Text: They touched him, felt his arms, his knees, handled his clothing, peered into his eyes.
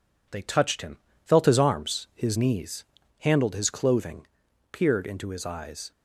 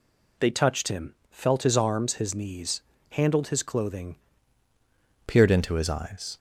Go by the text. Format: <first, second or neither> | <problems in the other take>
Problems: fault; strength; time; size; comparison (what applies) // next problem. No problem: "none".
first | changes voice at "peered"; from 5.2 s on; 1.1 s long